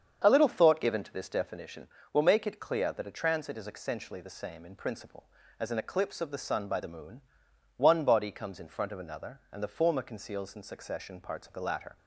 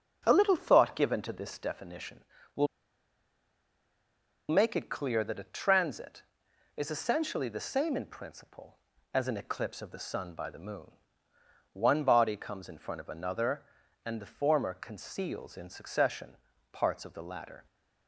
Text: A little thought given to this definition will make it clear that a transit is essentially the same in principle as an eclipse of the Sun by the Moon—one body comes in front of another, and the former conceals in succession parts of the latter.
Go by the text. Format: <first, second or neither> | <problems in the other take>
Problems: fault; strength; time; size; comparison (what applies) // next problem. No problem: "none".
first | starts louder than the rest; noticeable; until 1.2 s; 6 dB; strong in the first // pauses between "will" and "make"; strong; at 2.6 s; 1.8 s long // pauses between "succession" and "parts"; slight; at 16.3 s; 0.36 s long